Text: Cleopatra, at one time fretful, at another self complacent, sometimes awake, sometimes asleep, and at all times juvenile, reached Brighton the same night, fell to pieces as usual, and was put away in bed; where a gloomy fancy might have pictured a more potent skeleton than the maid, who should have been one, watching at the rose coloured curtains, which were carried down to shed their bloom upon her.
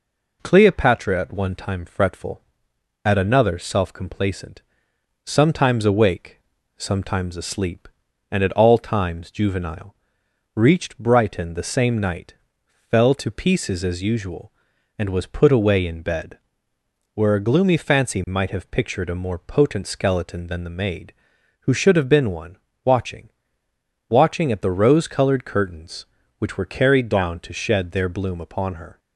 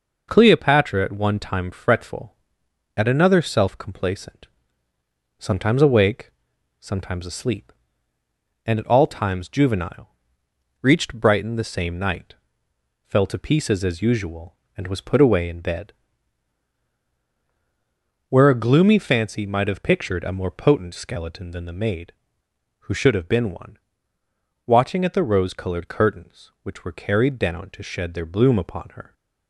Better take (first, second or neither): second